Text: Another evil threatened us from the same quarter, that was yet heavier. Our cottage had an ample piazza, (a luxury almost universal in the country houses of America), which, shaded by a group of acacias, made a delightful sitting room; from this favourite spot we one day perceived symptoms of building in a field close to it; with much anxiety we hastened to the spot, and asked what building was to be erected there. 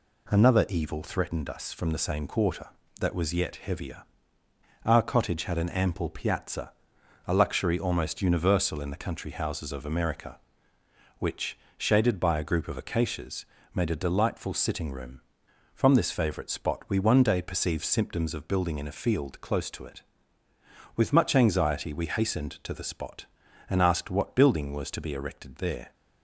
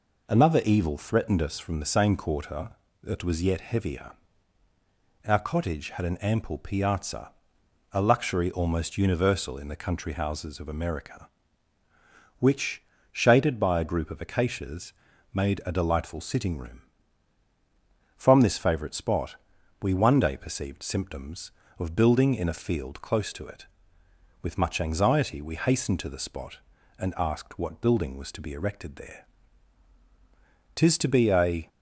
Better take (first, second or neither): first